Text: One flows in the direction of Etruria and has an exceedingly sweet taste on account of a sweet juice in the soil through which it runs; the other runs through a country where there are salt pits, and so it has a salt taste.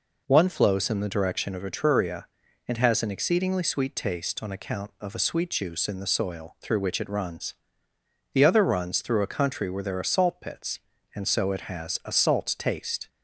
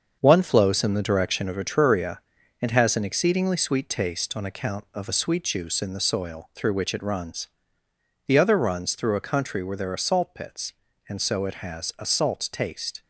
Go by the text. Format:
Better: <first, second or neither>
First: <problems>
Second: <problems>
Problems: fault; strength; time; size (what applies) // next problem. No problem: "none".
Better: first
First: none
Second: gets quieter; throughout; 7 dB